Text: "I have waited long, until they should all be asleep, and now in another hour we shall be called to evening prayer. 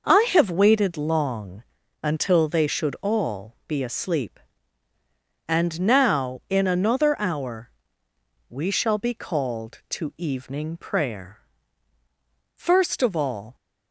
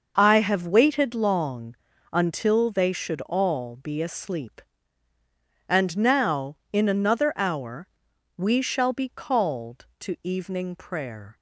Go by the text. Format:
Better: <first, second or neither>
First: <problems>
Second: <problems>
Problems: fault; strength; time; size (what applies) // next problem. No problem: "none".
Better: second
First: pauses between "hour" and "we"; noticeable; at 7.7 s; 0.76 s long // goes on to say "First of all"; noticeable; from 12.5 s on; 1.0 s long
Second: pauses between "hour" and "we"; noticeable; at 7.8 s; 0.52 s long